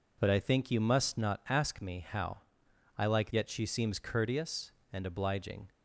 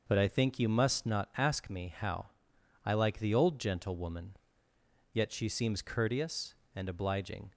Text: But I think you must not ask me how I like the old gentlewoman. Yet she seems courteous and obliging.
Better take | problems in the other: second | pauses between "how" and "I"; noticeable; at 2.3 s; 0.58 s long; noticeable in the second // skips "the old gentlewoman"; at 3.3 s

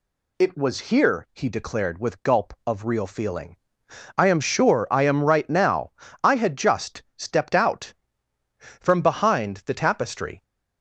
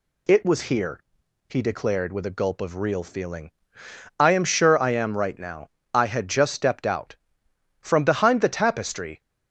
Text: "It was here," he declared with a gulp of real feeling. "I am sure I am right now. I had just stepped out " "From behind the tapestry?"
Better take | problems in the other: second | skips "a"; at 2.2 s

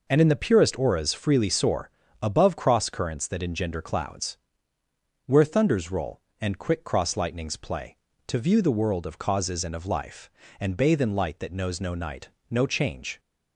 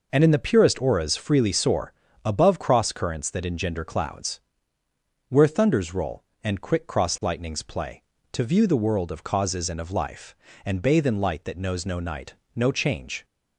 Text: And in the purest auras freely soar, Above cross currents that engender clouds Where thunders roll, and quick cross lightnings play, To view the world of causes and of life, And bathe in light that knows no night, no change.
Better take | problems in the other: neither | pauses between "clouds" and "Where"; noticeable; the same in both

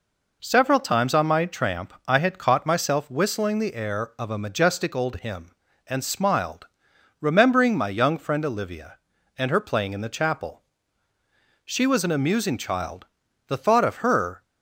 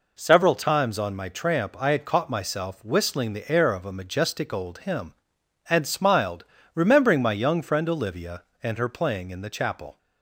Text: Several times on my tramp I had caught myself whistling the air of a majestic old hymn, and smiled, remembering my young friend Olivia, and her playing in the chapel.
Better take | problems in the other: second | pauses between "tramp" and "I"; slight; at 1.9 s; 0.16 s long // goes on to say "She was an amusing child the thought of her"; strong; from 11.6 s on; 2.7 s long

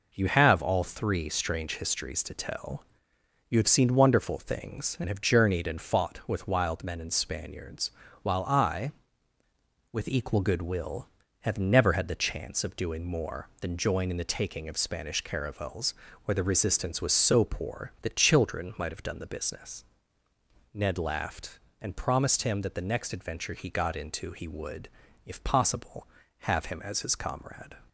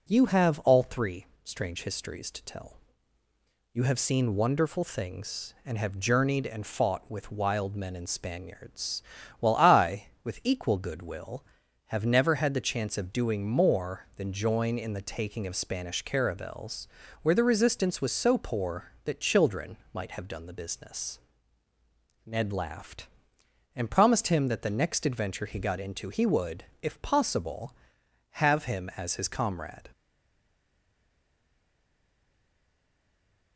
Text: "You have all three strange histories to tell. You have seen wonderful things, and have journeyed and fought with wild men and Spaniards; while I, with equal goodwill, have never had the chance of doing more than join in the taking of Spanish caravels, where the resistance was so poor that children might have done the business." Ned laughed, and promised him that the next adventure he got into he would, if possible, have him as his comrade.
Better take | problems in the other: first | pauses between "three" and "strange"; slight; at 1.2 s; 0.18 s long // pauses between "children" and "might"; slight; at 19.7 s; 0.16 s long // stays silent after the last word; strong; from 29.9 s on; 3.6 s long

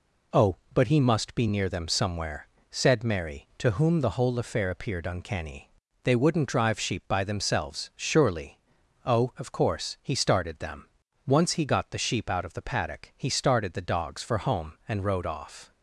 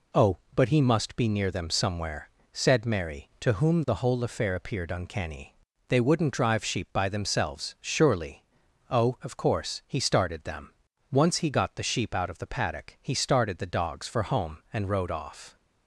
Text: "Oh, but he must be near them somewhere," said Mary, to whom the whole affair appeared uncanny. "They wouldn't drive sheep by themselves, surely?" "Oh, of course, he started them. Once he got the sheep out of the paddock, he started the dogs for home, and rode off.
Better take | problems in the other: neither | none

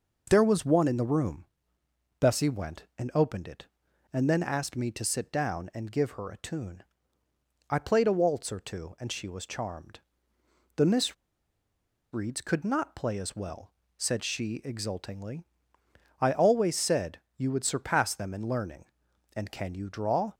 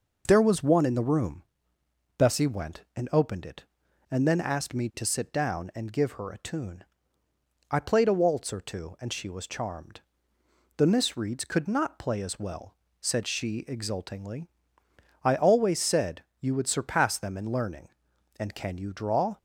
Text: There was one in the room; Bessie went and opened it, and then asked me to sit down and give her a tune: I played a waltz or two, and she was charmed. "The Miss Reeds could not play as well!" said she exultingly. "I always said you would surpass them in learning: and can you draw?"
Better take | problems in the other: second | pauses between "Miss" and "Reeds"; at 11.1 s; 0.98 s long // pauses between "said" and "you"; slight; at 17.1 s; 0.16 s long; slight in the second

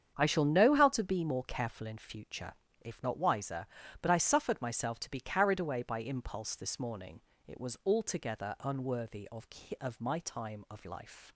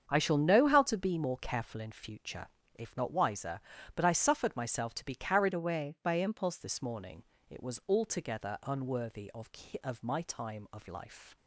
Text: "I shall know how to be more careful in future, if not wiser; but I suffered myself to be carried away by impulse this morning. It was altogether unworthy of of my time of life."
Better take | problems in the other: first | starts louder than the rest; strong; until 1.1 s; 7.5 dB; strong in the first // changes voice from "away" to "impulse"; from 5.5 to 6.5 s; 1.0 s long

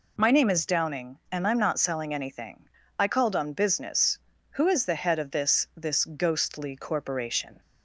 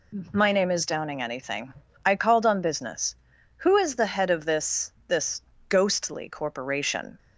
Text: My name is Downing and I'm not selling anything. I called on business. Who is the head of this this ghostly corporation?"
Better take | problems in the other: first | skips "and I'm not selling"; at 1.2 s // pauses between "this" and "this"; slight; at 4.9 s; 0.16 s long // pauses between "this" and "ghostly"; slight; at 5.4 s; 0.28 s long

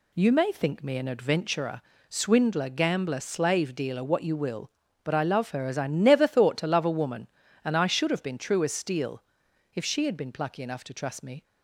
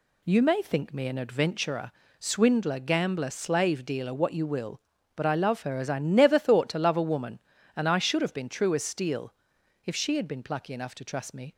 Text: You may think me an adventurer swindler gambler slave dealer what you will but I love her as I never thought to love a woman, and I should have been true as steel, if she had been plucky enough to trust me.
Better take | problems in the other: neither | pauses between "adventurer" and "swindler"; slight; the same in both

